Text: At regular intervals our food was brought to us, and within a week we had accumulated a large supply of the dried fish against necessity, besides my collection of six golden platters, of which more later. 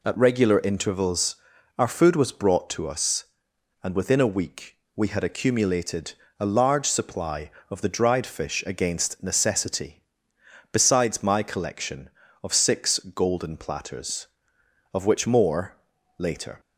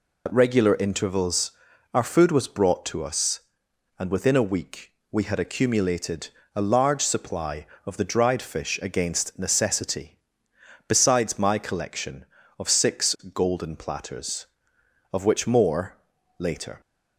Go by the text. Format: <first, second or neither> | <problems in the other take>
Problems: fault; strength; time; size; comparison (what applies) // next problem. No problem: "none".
first | loses the start of "At"; at 0.2 s; 70 ms // pauses between "intervals" and "our"; at 1.5 s; 0.42 s long; also in the first // pauses between "week" and "we"; slight; at 4.9 s; 0.18 s long; slight in the first // pauses between "accumulated" and "a"; slight; at 6.2 s; 0.26 s long; slight in the first // pauses between "more" and "later"; at 15.9 s; 0.42 s long; also in the first